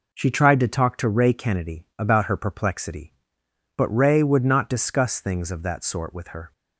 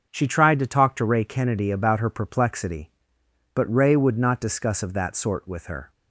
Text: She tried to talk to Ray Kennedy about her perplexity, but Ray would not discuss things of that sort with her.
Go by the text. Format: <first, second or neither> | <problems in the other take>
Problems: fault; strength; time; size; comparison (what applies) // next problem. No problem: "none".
first | starts louder than the rest; until 1.1 s; 6 dB // skips "things"; at 4.8 s